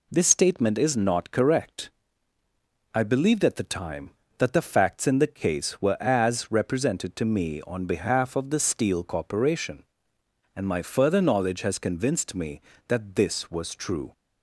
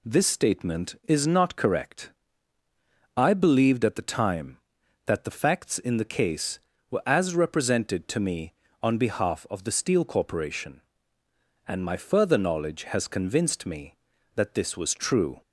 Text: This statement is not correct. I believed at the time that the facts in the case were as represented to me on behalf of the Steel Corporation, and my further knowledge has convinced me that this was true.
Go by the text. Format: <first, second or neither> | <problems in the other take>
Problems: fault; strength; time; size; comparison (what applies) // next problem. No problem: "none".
neither | none